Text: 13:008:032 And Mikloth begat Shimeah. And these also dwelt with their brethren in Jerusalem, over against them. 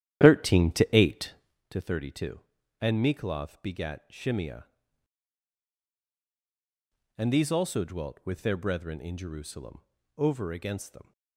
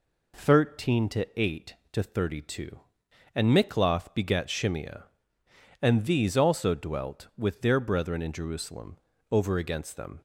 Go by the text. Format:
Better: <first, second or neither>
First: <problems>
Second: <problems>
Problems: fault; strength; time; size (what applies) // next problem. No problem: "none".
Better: second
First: starts louder than the rest; strong; until 1.6 s; 11 dB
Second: none